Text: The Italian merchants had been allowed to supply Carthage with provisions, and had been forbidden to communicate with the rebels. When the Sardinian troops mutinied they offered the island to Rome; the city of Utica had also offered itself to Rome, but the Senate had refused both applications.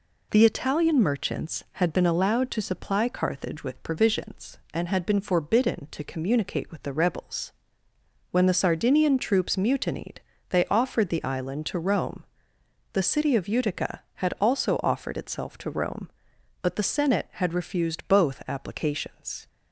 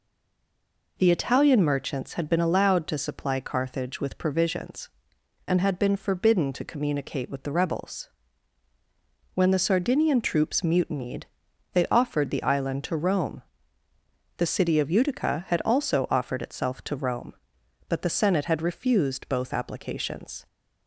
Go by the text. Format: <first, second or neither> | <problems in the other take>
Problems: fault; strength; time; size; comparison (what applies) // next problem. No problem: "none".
first | stays silent before the first word; until 0.9 s; 0.9 s long // pauses between "mutinied" and "they"; noticeable; at 11.2 s; 0.48 s long; slight in the first